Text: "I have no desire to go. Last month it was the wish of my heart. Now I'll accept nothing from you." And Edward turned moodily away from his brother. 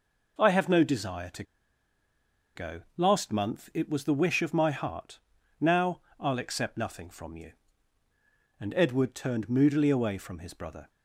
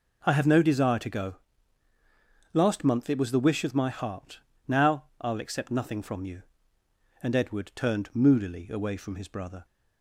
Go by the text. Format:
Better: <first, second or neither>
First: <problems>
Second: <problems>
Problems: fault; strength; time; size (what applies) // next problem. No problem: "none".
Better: second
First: pauses between "to" and "go"; at 1.4 s; 1.1 s long // pauses between "Now" and "I'll"; slight; at 6.0 s; 0.18 s long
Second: pauses between "Now" and "I'll"; slight; at 5.0 s; 0.16 s long